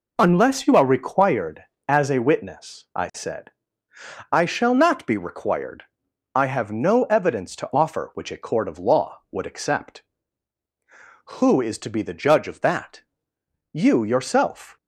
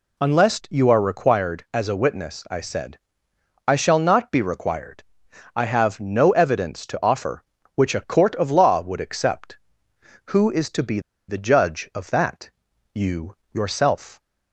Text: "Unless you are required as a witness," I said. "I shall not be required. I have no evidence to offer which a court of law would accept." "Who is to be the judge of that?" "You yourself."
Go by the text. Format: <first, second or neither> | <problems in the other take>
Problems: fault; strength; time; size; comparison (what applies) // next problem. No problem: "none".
first | pauses between "be" and "the"; slight; at 10.9 s; 0.29 s long // pauses between "You" and "yourself"; slight; at 13.3 s; 0.18 s long